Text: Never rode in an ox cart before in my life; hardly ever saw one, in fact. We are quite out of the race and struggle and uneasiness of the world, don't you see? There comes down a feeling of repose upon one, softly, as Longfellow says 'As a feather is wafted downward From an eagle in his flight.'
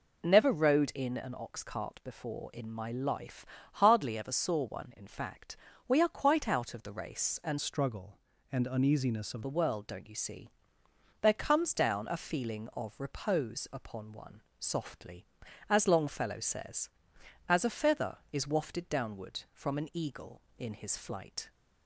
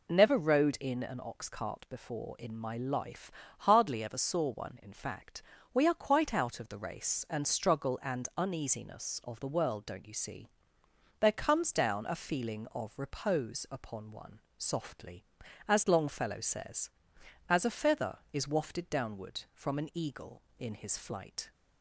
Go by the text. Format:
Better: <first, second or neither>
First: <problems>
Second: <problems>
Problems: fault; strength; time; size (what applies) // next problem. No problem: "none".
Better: second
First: changes voice from "struggle" to "of"; from 7.6 to 9.4 s; 1.8 s long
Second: none